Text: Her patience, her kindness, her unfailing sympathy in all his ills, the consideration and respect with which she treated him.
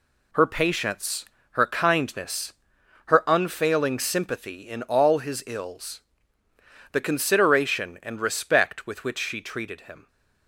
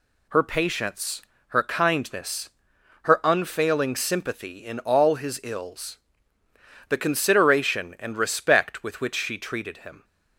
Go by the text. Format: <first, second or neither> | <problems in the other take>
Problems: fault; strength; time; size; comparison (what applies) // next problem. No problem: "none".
second | gets quieter; strong; throughout; 7.5 dB